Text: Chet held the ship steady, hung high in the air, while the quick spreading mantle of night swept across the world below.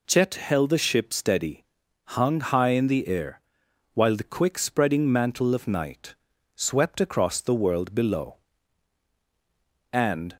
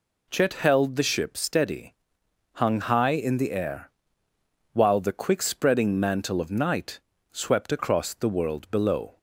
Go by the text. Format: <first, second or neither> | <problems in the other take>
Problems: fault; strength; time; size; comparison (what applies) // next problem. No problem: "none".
second | pauses between "night" and "swept"; at 6.1 s; 0.40 s long; slight in the second // goes on to say "And"; slight; from 9.9 s on; 0.44 s long